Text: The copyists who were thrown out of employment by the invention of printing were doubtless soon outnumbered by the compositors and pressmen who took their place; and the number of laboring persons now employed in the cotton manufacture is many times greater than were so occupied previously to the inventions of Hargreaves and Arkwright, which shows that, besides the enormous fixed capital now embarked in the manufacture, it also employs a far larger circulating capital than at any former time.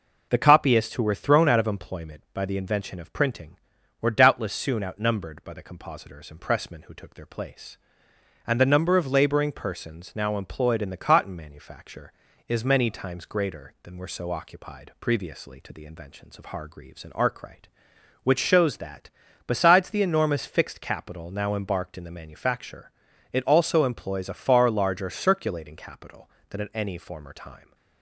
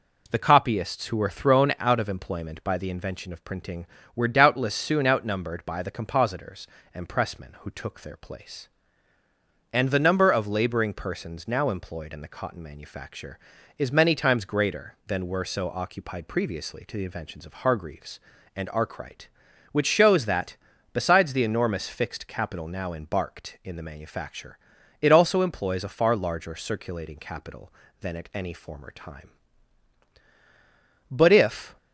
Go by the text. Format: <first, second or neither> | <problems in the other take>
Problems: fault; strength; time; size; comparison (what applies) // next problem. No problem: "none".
first | goes on to say "But if"; noticeable; from 31.0 s on; 0.68 s long